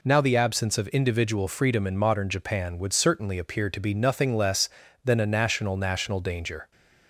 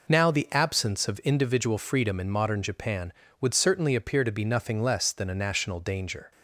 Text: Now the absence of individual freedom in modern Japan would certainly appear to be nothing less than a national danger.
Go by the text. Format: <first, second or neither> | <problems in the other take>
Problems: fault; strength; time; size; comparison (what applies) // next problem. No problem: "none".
second | says "national" twice; at 5.7 s